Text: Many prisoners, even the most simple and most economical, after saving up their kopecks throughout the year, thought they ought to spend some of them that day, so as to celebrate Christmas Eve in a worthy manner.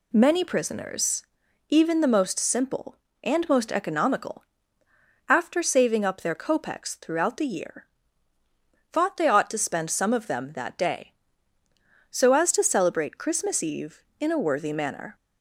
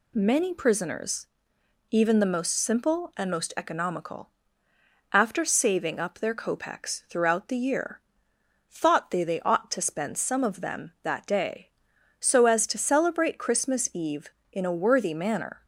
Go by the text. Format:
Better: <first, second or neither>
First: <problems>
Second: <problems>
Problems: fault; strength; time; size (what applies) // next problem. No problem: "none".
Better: first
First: none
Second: says "they" twice; at 9.2 s